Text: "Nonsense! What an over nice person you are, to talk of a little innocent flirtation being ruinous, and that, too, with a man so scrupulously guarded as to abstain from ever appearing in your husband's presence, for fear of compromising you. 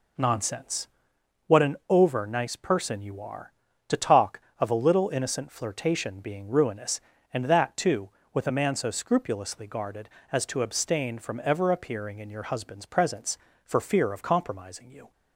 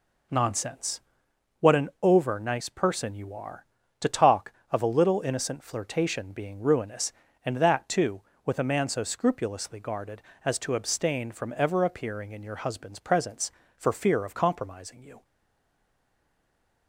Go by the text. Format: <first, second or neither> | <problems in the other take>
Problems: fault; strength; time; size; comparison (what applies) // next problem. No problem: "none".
first | stays silent after the last word; noticeable; from 15.2 s on; 1.6 s long